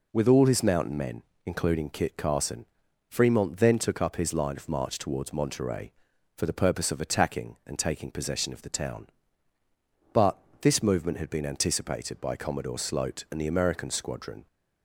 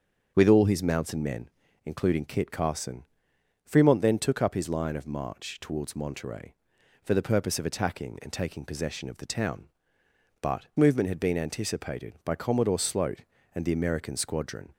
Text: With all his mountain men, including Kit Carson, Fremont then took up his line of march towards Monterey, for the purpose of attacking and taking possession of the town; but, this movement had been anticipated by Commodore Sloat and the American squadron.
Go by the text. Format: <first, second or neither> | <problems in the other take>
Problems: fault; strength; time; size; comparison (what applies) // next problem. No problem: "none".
first | starts louder than the rest; until 1.3 s; 7 dB // skips "this"; at 10.7 s